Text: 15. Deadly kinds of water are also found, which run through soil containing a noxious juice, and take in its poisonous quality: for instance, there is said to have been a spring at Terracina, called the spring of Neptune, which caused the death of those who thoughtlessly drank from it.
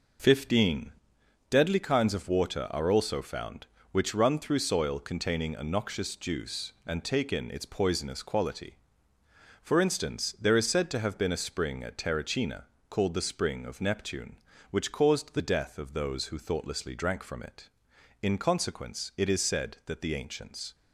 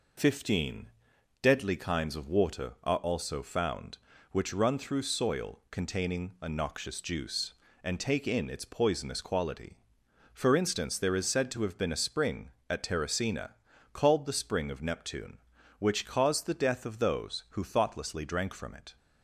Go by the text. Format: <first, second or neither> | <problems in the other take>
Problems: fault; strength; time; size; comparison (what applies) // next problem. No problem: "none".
second | goes on to say "In consequence it is said that the ancients"; strong; from 18.2 s on; 2.5 s long